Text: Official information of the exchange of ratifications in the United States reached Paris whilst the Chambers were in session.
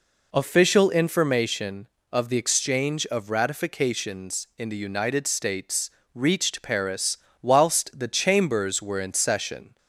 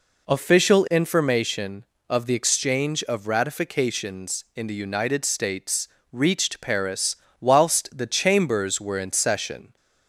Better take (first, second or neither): neither